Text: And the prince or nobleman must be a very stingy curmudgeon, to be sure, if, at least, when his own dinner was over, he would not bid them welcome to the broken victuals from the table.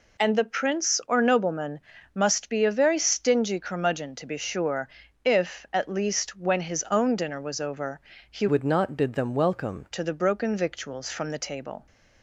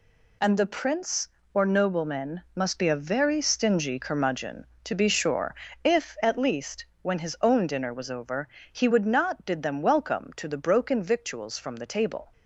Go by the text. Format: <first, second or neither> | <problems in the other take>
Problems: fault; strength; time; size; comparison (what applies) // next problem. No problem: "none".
second | pauses between "nobleman" and "must"; slight; at 1.7 s; 0.36 s long // changes voice from "would" to "welcome"; from 8.4 to 9.8 s; 1.4 s long